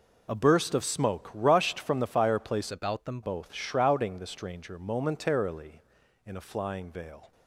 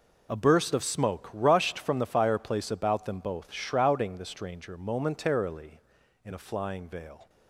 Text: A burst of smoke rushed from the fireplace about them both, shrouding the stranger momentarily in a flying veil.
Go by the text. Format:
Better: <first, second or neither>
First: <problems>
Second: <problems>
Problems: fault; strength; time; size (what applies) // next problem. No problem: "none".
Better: second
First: changes voice from "about" to "them"; from 2.7 to 3.2 s; 0.5 s long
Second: none